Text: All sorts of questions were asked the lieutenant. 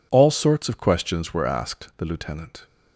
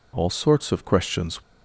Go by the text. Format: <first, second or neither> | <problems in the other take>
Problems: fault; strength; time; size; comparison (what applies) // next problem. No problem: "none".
first | stops before "were asked the lieutenant"; at 1.4 s